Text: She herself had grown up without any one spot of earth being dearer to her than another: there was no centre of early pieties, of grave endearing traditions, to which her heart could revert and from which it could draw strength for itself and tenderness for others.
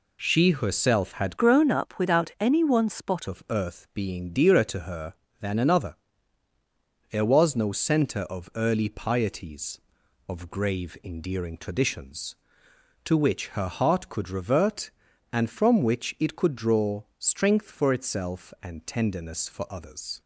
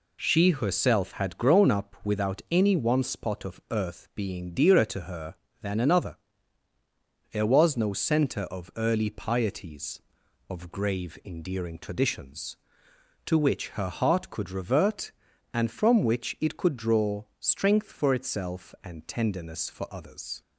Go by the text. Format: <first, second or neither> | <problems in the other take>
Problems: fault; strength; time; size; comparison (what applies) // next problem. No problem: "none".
second | changes voice from "grown" to "spot"; from 1.3 to 3.2 s; 1.9 s long // pauses between "draw" and "strength"; slight; at 17.0 s; 0.16 s long; slight in the second